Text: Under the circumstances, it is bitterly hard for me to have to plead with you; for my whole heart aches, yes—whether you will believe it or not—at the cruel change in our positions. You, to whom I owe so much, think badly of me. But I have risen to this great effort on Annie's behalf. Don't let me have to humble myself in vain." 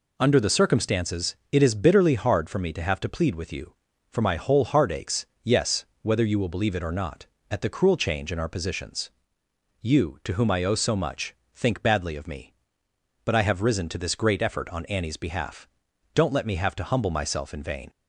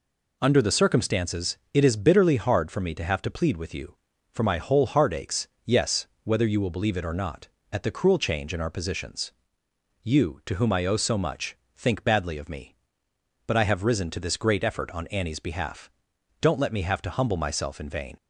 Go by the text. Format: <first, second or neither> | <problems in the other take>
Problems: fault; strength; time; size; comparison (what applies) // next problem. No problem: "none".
neither | none